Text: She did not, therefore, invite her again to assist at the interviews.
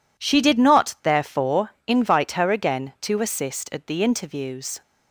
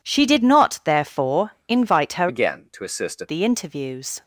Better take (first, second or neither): first